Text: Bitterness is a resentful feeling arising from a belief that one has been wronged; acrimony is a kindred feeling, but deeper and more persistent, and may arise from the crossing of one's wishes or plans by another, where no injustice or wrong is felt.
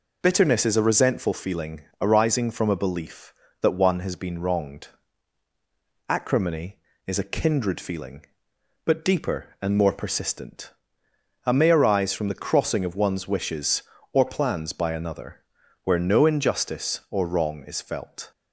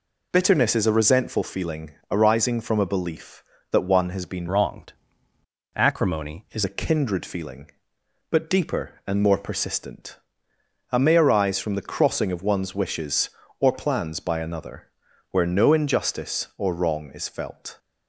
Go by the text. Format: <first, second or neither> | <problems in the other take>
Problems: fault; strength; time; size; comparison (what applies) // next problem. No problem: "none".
first | pauses between "feeling" and "arising"; slight; at 1.9 s; 0.20 s long; slight in the first // changes voice from "wronged" to "is"; from 4.4 to 6.6 s; 2.2 s long